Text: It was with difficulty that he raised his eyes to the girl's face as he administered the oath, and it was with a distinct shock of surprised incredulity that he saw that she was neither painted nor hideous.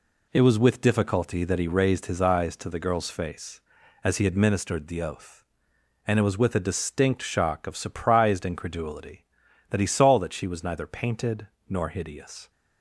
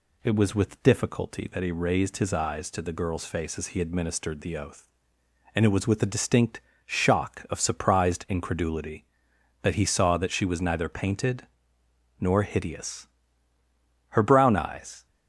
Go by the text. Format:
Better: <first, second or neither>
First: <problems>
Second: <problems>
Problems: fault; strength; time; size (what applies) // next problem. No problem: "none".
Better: first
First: pauses between "painted" and "nor"; slight; at 11.4 s; 0.20 s long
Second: pauses between "distinct" and "shock"; slight; at 6.5 s; 0.26 s long // pauses between "painted" and "nor"; noticeable; at 11.4 s; 0.74 s long // goes on to say "Her brown eyes"; noticeable; from 14.0 s on; 0.96 s long